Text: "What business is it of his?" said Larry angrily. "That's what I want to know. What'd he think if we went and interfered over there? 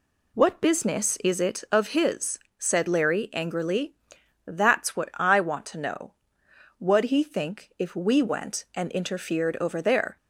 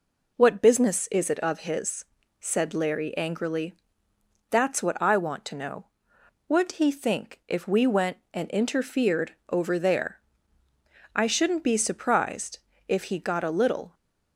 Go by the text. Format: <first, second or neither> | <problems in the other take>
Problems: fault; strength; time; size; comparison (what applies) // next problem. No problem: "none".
first | goes on to say "I shouldn't be surprised if he got a little"; strong; from 11.1 s on; 2.8 s long